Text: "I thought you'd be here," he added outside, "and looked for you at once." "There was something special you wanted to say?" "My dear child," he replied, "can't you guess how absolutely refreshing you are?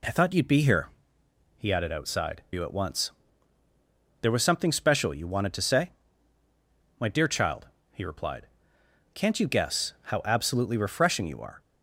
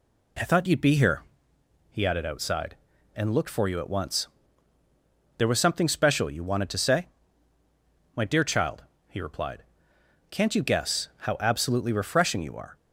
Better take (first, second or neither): second